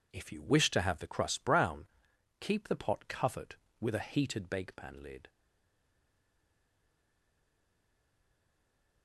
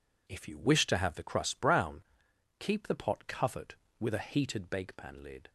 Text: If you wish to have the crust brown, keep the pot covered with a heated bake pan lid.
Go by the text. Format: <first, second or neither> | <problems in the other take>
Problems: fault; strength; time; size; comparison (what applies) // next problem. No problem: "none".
second | stays silent after the last word; strong; from 5.2 s on; 3.8 s long